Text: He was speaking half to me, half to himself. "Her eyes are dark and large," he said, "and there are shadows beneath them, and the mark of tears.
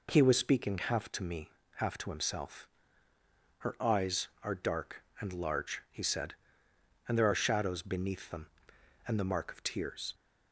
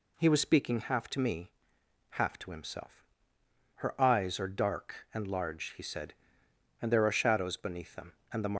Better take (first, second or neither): first